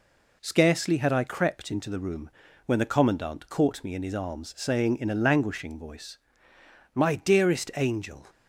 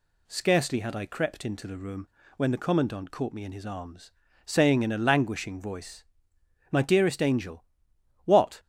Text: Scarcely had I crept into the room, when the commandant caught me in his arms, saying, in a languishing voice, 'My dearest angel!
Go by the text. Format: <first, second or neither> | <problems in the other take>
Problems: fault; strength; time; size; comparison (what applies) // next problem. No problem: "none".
first | goes on to say "what"; slight; from 8.2 s on; 0.34 s long